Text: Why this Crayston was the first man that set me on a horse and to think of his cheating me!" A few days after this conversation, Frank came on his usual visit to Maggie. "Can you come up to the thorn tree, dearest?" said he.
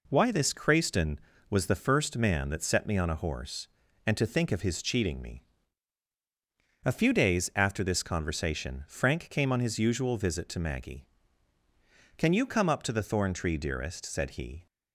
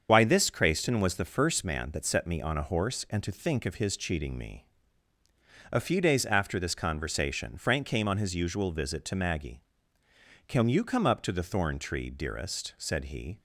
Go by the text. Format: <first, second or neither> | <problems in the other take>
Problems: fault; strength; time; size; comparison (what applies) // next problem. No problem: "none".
first | loses the start of "Why"; at 0.0 s; 50 ms // starts louder than the rest; strong; until 1.1 s; 7 dB